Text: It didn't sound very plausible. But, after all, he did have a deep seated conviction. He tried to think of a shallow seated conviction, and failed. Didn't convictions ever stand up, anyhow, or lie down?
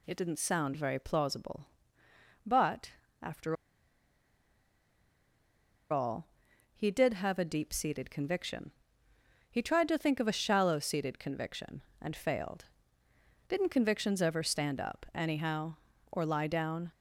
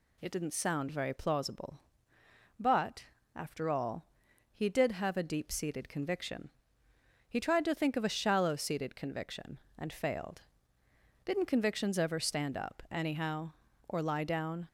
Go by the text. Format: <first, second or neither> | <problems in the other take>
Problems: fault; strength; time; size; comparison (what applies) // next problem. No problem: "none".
second | pauses between "after" and "all"; strong; at 3.5 s; 2.3 s long